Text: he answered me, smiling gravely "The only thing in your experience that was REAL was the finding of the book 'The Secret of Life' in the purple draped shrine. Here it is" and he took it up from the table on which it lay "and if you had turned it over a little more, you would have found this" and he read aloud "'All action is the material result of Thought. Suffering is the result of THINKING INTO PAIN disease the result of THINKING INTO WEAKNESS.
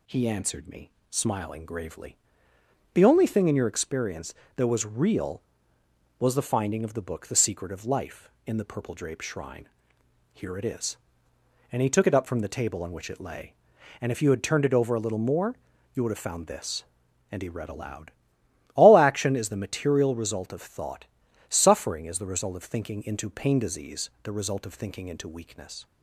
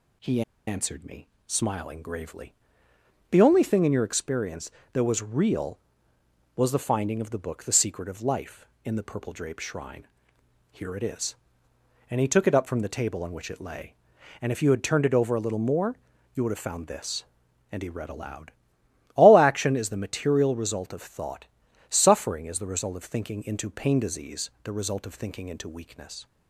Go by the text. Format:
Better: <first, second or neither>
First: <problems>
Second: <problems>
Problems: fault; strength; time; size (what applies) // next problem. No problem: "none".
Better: first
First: pauses between "gravely" and "The"; noticeable; at 2.1 s; 0.78 s long // pauses between "aloud" and "All"; noticeable; at 18.1 s; 0.64 s long // pauses between "disease" and "the"; slight; at 24.0 s; 0.16 s long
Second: pauses between "he" and "answered"; slight; at 0.4 s; 0.25 s long // pauses between "gravely" and "The"; noticeable; at 2.5 s; 0.78 s long // pauses between "aloud" and "All"; noticeable; at 18.5 s; 0.64 s long // pauses between "disease" and "the"; slight; at 24.4 s; 0.16 s long